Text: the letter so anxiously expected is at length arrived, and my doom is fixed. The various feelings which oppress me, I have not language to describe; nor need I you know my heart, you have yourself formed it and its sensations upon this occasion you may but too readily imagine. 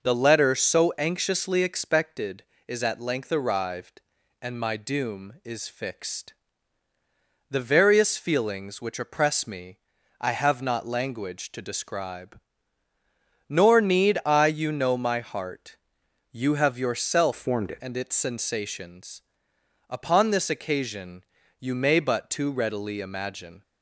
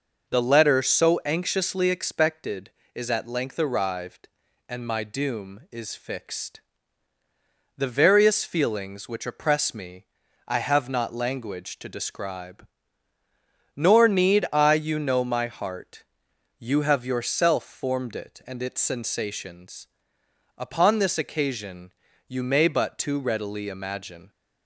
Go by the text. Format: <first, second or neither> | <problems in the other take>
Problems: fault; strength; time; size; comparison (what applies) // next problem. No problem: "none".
second | changes voice from "formed" to "it"; from 17.3 to 17.8 s; 0.5 s long // pauses between "sensations" and "upon"; noticeable; at 19.1 s; 0.70 s long; noticeable in the second // pauses between "occasion" and "you"; at 21.2 s; 0.38 s long; also in the second